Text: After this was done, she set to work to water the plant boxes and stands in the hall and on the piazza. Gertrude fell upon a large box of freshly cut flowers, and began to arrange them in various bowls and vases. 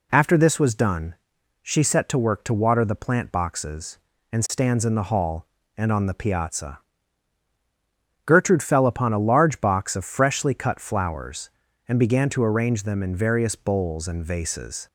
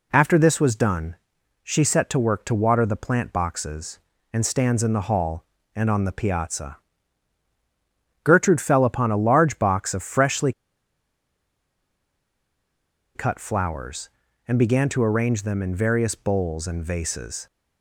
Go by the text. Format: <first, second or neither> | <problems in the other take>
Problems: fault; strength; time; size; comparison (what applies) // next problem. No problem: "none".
first | pauses between "freshly" and "cut"; strong; at 10.5 s; 2.6 s long